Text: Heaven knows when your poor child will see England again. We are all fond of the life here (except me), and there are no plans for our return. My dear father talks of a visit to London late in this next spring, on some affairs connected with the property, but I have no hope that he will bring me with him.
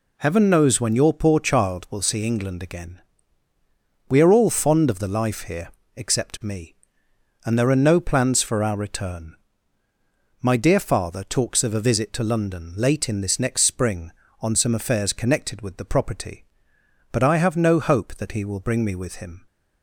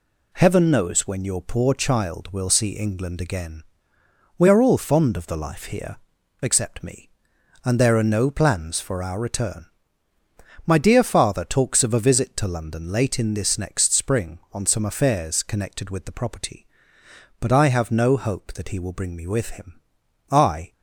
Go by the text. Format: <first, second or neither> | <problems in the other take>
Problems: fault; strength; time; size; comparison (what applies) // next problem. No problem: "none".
first | goes on to say "I"; slight; from 20.3 s on; 0.42 s long